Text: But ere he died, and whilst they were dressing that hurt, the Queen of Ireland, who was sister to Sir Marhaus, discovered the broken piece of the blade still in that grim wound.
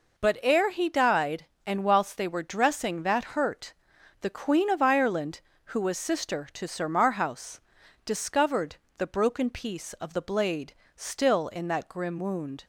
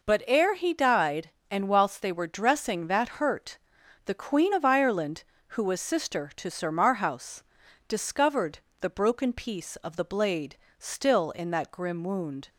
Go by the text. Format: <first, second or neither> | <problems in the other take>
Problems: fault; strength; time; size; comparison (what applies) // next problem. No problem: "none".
neither | pauses between "discovered" and "the"; slight; the same in both // pauses between "blade" and "still"; slight; the same in both